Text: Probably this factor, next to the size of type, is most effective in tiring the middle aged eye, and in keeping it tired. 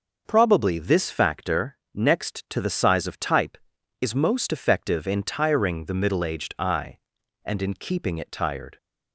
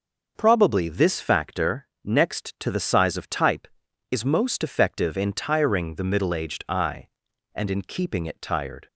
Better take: neither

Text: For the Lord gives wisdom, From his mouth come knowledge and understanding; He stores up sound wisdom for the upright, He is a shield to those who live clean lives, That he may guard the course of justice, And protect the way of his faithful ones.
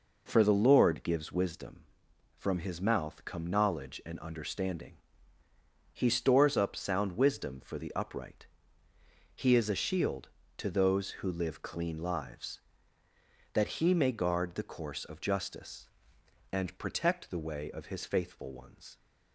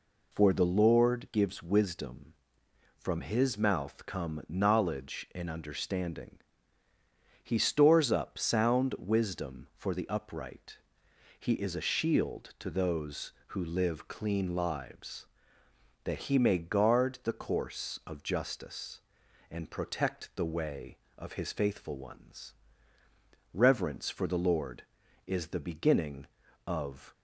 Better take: first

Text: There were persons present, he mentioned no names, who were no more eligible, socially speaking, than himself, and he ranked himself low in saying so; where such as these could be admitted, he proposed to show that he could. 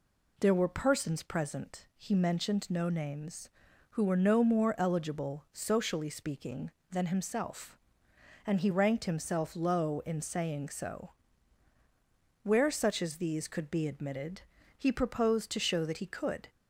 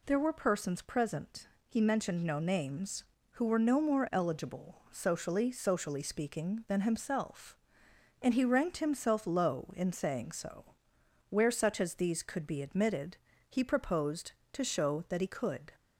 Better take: first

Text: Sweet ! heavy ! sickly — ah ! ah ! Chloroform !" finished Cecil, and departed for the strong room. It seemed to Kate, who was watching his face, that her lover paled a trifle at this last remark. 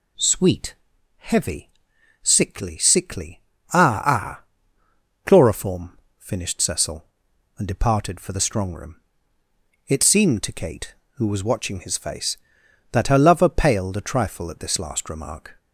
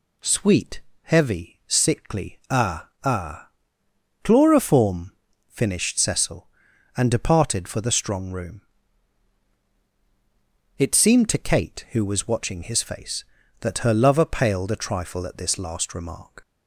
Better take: second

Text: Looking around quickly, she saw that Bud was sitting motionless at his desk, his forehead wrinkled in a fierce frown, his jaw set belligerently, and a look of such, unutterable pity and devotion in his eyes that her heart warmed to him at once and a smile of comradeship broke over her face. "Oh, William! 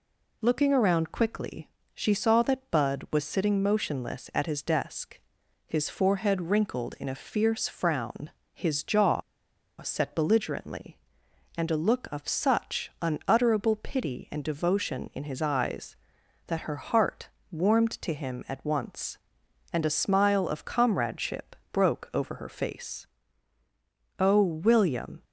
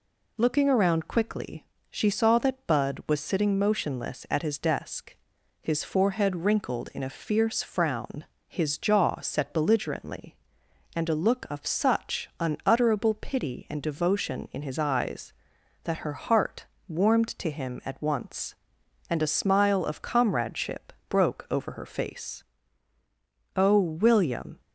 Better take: second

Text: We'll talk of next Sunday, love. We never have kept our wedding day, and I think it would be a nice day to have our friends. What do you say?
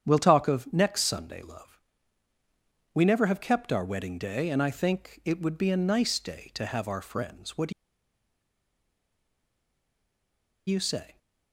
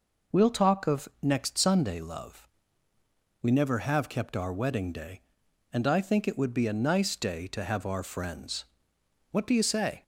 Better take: second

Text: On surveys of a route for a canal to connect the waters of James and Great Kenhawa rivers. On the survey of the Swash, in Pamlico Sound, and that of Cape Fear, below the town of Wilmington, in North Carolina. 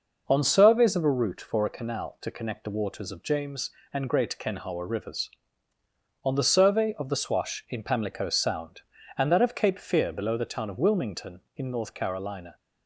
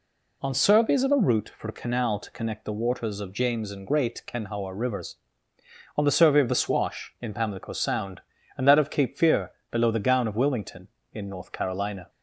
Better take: first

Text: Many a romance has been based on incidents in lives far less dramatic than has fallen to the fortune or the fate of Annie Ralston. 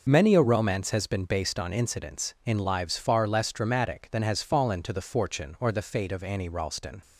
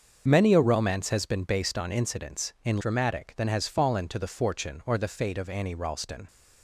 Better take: first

